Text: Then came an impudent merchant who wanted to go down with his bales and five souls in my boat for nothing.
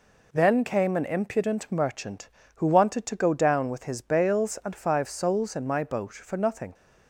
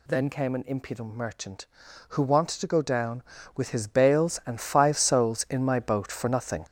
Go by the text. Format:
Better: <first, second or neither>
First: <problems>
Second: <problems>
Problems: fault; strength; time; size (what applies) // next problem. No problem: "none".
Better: first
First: none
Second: gets louder; strong; throughout; 7.5 dB